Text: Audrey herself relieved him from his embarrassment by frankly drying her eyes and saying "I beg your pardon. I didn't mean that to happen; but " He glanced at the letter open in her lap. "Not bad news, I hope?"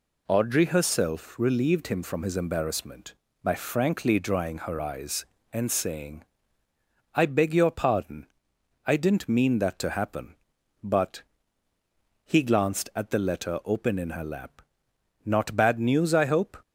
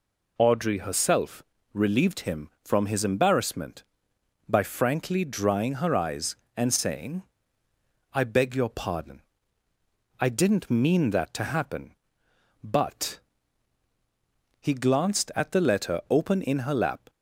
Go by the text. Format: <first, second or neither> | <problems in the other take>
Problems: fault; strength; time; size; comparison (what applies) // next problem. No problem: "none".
first | pauses between "herself" and "relieved"; slight; at 1.4 s; 0.28 s long // pauses between "saying" and "I"; noticeable; at 7.2 s; 0.92 s long; noticeable in the first // stops before "Not bad news I hope"; at 17.0 s